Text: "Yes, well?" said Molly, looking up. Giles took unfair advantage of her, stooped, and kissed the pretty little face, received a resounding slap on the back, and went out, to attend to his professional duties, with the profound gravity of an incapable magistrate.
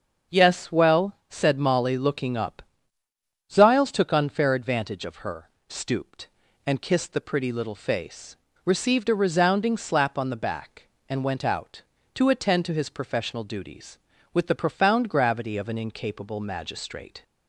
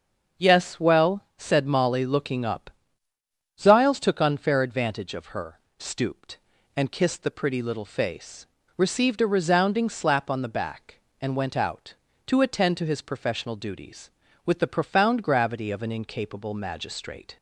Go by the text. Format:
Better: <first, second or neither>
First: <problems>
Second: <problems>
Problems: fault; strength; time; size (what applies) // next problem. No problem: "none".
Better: neither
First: starts louder than the rest; until 1.4 s; 6.5 dB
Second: starts louder than the rest; until 1.5 s; 6.5 dB